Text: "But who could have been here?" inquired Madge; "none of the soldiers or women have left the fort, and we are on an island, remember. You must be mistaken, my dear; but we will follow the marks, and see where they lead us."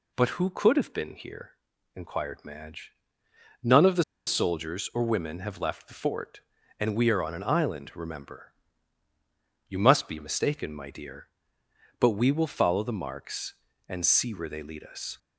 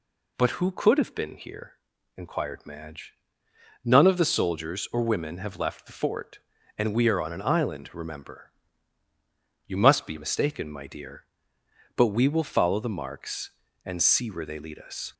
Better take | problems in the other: second | pauses between "the" and "soldiers"; slight; at 4.0 s; 0.23 s long

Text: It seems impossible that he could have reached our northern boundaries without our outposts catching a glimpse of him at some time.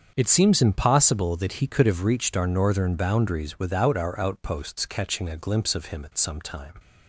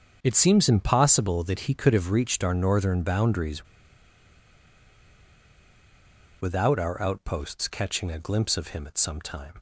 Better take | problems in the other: first | starts louder than the rest; strong; until 1.2 s; 7 dB; strong in the first // pauses between "boundaries" and "without"; strong; at 3.6 s; 2.7 s long

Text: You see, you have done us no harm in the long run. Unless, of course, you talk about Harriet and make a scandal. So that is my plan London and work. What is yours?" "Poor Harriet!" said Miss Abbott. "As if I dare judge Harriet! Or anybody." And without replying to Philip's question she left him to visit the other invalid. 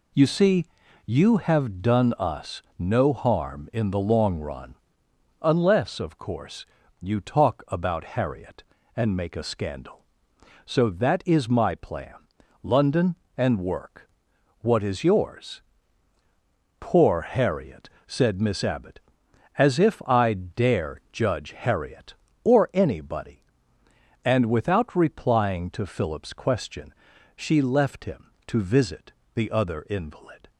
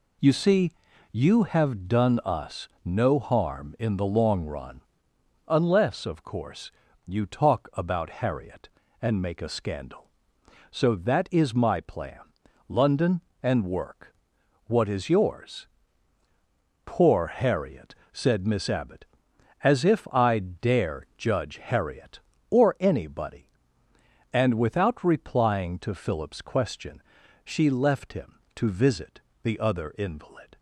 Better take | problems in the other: neither | pauses between "us" and "no"; slight; the same in both // pauses between "plan" and "London"; noticeable; the same in both // pauses between "question" and "she"; the same in both // pauses between "visit" and "the"; slight; the same in both

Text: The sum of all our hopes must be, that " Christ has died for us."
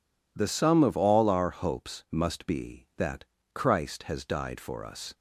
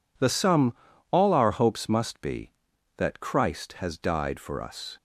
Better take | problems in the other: first | skips "of"; at 0.9 s

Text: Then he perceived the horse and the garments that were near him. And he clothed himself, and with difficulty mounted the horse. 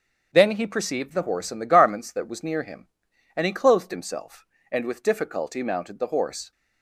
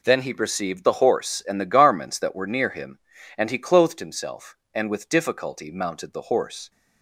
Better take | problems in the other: second | starts louder than the rest; until 1.3 s; 7 dB // says "was" for "were"; at 2.2 s

